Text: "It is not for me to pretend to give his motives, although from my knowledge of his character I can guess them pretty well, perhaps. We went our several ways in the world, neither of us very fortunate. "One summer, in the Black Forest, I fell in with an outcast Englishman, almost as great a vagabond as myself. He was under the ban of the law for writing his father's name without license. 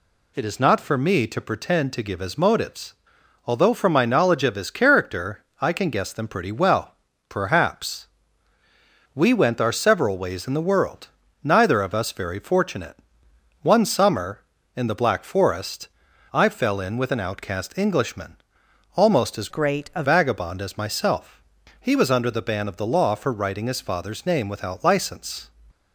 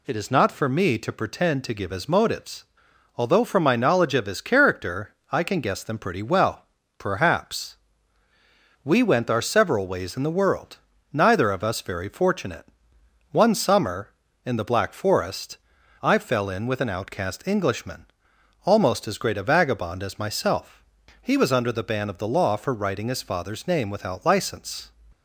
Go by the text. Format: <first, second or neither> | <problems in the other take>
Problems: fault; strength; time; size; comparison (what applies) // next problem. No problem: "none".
second | pauses between "character" and "I"; slight; at 5.4 s; 0.18 s long; slight in the second // changes voice from "great" to "a"; from 19.4 to 20.0 s; 0.6 s long